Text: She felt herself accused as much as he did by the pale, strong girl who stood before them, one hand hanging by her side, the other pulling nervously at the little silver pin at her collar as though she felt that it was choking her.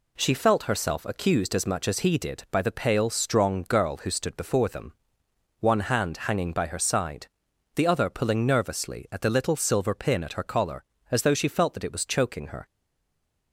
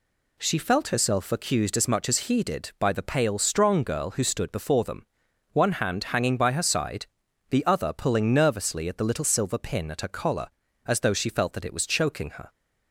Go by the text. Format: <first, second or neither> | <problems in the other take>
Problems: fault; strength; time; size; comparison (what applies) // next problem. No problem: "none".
second | stays silent after the last word; slight; from 12.6 s on; 0.9 s long